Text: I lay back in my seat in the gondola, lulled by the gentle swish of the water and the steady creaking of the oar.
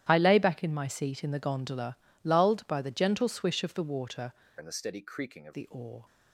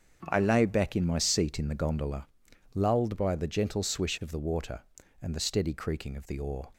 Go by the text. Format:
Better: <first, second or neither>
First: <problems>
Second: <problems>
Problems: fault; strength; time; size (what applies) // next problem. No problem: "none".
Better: second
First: starts louder than the rest; strong; until 1.1 s; 11.5 dB // changes voice from "and" to "of"; from 4.5 to 5.5 s; 1.0 s long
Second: starts louder than the rest; strong; until 1.3 s; 7.5 dB